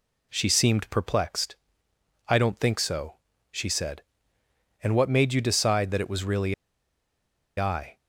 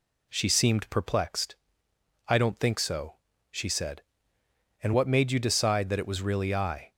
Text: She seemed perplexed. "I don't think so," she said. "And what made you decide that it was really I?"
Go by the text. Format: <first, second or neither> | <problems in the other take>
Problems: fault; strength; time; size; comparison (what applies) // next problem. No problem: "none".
second | pauses between "really" and "I"; at 6.5 s; 1.0 s long